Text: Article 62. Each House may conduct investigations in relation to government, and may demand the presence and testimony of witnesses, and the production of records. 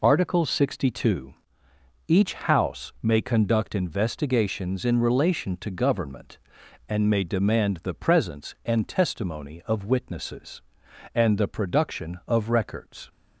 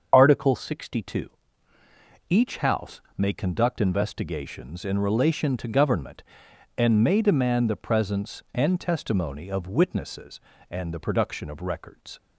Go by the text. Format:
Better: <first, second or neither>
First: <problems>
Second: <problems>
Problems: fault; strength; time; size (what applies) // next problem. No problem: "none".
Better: first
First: none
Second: loses the start of "Article"; at 0.1 s; 45 ms // starts louder than the rest; until 1.1 s; 6.5 dB // pauses between "House" and "may"; slight; at 2.9 s; 0.16 s long